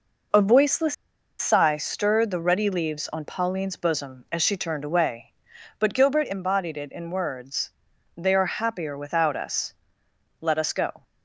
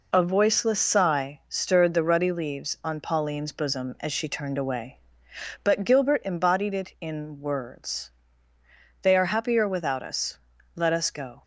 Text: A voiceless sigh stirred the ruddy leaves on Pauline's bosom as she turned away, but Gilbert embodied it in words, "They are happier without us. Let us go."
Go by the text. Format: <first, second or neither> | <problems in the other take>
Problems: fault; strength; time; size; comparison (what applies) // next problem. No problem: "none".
second | pauses between "voiceless" and "sigh"; at 0.9 s; 0.44 s long